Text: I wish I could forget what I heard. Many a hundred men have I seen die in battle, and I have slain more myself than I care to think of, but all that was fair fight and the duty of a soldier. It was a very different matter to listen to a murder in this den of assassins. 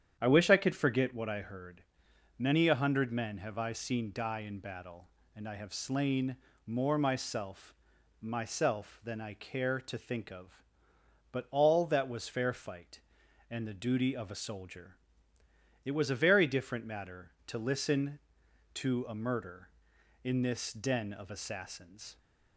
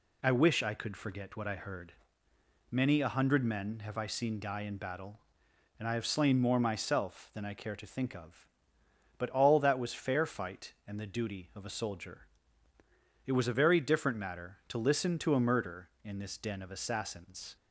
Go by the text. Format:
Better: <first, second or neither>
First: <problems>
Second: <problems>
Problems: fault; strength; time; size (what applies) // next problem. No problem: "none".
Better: second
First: starts louder than the rest; strong; until 1.2 s; 9 dB // pauses between "slain" and "more"; slight; at 6.3 s; 0.28 s long // says "myself" twice; at 8.1 s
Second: none